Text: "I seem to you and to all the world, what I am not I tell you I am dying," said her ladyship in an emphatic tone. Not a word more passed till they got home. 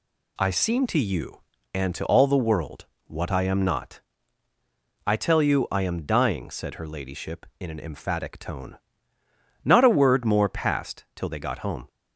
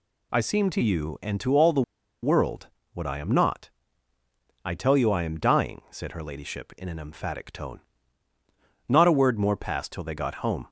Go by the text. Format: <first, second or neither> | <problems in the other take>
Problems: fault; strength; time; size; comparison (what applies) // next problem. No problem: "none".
first | pauses between "the" and "world"; at 1.8 s; 0.40 s long // pauses between "not" and "I"; noticeable; at 3.6 s; 0.96 s long; also in the first